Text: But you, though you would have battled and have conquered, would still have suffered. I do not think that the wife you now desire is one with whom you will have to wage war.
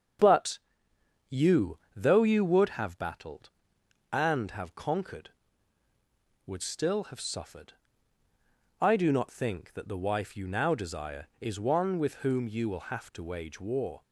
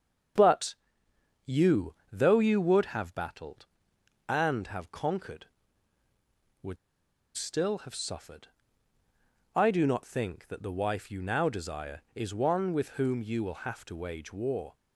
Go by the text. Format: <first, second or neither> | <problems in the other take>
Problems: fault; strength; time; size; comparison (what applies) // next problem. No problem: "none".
first | starts louder than the rest; until 2.2 s; 7 dB; also in the first // pauses between "But" and "you"; noticeable; at 0.7 s; 0.72 s long; noticeable in the first // pauses between "would" and "still"; noticeable; at 6.7 s; 0.58 s long